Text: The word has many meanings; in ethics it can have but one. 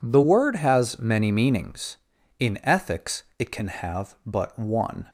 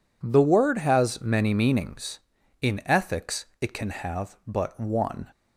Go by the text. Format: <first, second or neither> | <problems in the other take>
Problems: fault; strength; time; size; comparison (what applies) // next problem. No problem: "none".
neither | none